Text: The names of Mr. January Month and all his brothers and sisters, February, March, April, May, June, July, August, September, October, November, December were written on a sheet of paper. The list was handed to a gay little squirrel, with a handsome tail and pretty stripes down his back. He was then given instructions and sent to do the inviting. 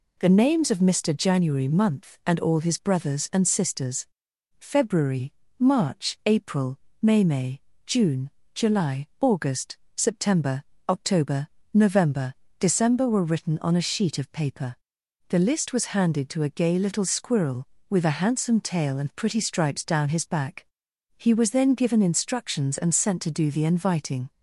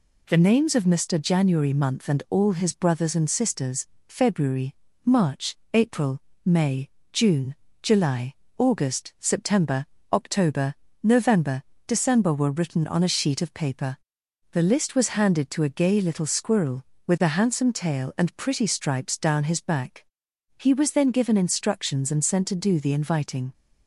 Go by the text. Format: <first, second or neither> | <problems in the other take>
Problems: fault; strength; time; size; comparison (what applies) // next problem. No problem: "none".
second | says "May" twice; at 7.2 s